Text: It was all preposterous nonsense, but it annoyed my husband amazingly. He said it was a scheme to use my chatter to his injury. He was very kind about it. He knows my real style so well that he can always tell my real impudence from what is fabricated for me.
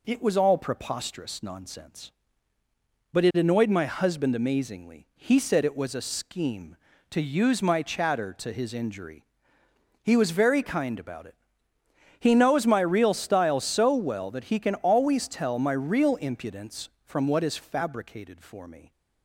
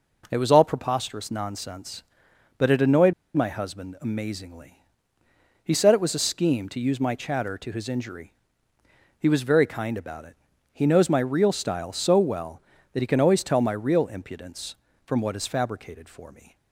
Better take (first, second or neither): first